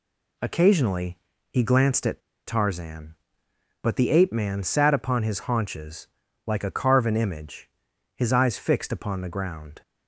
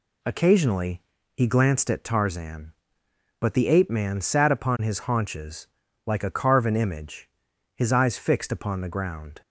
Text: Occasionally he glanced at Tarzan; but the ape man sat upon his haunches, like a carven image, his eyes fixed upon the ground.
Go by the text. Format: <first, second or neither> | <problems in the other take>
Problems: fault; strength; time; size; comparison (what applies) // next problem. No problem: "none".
second | pauses between "Occasionally" and "he"; slight; at 1.1 s; 0.34 s long; slight in the second // pauses between "at" and "Tarzan"; slight; at 2.1 s; 0.27 s long